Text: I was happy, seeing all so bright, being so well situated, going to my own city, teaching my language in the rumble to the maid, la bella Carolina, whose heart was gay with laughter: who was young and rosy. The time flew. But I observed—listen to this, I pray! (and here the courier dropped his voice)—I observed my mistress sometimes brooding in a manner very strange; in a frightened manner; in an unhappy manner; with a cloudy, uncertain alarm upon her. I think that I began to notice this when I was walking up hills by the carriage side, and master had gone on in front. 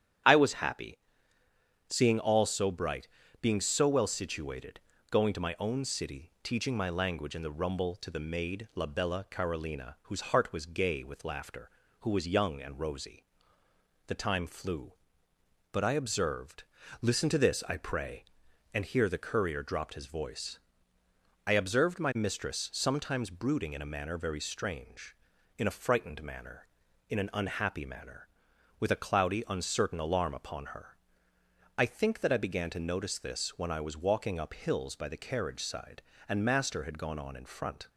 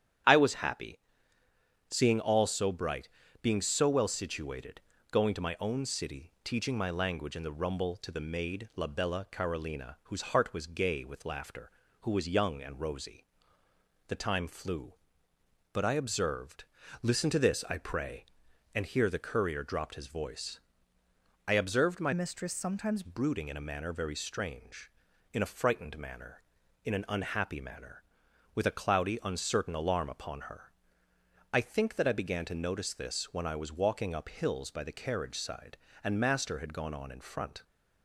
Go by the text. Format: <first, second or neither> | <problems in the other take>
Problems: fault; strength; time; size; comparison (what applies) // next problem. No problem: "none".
first | starts louder than the rest; strong; until 2.2 s; 10 dB; strong in the first // changes voice from "mistress" to "sometimes"; from 22.1 to 23.0 s; 0.9 s long